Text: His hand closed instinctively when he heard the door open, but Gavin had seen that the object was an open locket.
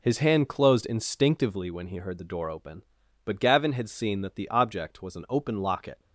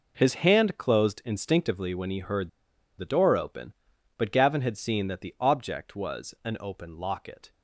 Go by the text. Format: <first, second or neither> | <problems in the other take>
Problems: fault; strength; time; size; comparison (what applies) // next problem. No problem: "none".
first | pauses between "heard" and "the"; noticeable; at 2.4 s; 0.48 s long